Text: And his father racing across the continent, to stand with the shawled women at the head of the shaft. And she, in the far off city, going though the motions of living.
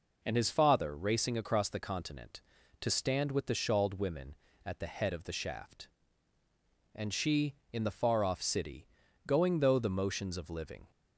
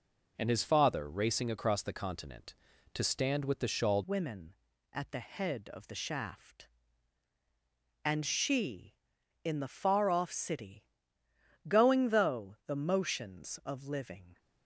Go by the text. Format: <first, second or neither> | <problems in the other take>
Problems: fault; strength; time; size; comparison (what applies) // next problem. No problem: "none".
first | changes voice at "women"; from 4.0 s on; 10.3 s long